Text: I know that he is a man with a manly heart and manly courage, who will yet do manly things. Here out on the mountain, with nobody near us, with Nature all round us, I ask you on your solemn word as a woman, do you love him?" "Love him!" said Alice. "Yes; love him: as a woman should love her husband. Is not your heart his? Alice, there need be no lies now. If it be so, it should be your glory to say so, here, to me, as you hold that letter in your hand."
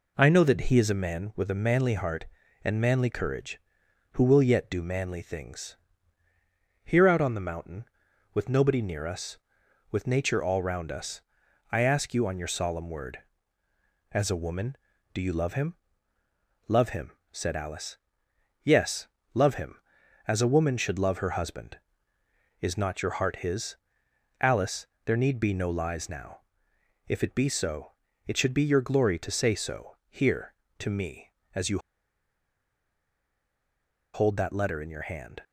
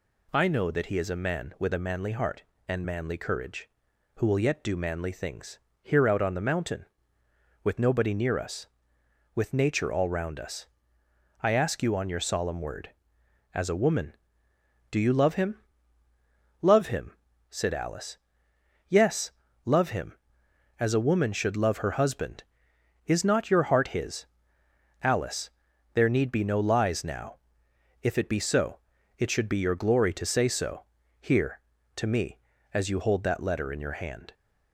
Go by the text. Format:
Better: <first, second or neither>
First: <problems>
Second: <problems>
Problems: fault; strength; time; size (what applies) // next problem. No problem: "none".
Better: second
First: pauses between "you" and "hold"; strong; at 31.7 s; 2.3 s long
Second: none